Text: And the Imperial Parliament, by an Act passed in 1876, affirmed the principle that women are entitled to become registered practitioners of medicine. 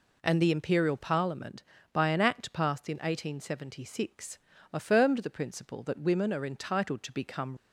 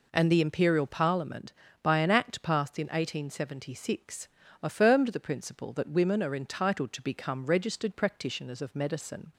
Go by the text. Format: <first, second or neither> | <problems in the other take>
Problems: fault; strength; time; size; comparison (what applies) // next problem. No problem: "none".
second | stops before "registered practitioners of medicine"; at 7.5 s